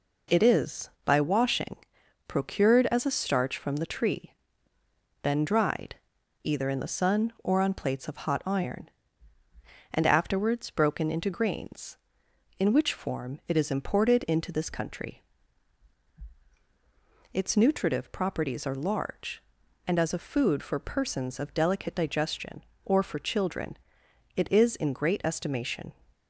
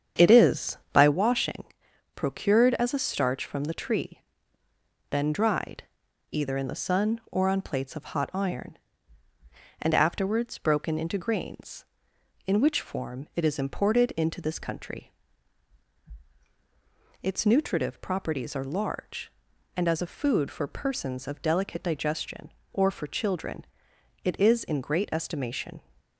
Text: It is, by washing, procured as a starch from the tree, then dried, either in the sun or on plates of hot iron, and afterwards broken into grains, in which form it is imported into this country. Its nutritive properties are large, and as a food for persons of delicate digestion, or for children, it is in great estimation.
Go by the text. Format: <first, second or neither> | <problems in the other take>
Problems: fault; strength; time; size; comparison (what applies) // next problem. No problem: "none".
first | starts louder than the rest; strong; until 1.2 s; 8 dB